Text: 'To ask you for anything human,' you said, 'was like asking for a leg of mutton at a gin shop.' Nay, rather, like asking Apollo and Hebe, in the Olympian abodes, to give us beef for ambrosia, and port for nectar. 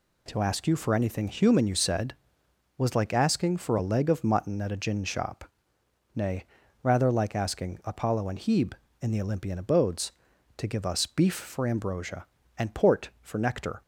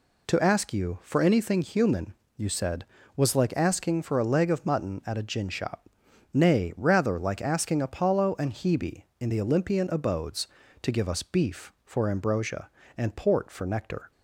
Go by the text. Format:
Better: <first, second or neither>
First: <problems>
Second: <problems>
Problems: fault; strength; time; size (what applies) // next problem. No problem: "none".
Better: neither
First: none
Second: none